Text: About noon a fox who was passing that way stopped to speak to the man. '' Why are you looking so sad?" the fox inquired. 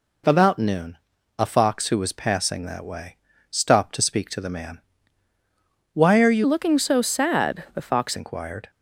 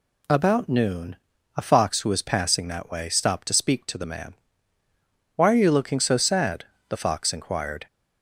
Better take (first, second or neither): second